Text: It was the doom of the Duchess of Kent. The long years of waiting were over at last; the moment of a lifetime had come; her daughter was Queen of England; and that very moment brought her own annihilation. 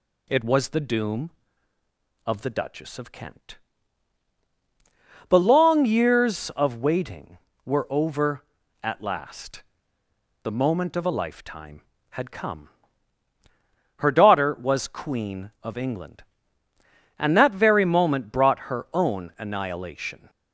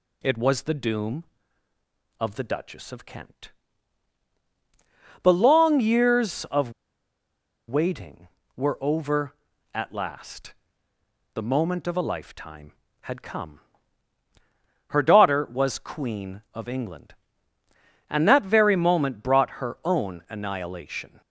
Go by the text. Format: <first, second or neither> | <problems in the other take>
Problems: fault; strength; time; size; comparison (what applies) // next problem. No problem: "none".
first | pauses between "of" and "waiting"; noticeable; at 6.7 s; 0.95 s long